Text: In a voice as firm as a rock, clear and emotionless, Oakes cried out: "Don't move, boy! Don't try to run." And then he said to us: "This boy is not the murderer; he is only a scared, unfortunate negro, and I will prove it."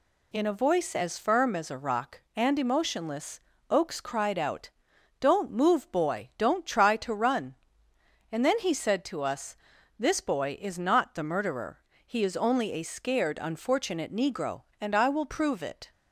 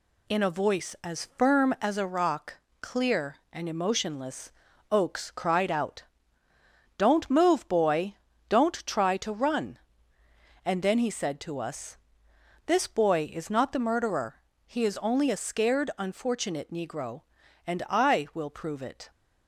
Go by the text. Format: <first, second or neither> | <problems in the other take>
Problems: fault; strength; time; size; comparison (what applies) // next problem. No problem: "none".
second | skips "clear"; at 2.2 s